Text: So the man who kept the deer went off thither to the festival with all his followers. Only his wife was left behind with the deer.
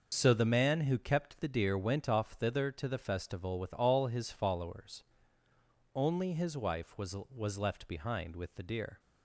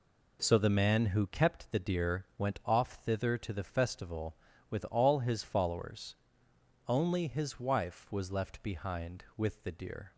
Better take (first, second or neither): second